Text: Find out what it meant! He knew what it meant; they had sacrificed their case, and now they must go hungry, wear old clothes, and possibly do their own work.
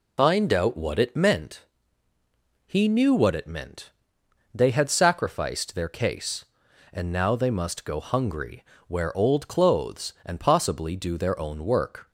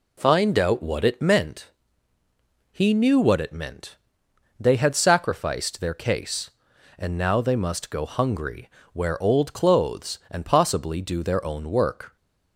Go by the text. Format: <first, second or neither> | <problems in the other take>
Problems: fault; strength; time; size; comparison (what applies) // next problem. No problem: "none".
second | loses the start of "Find"; at 0.1 s; 60 ms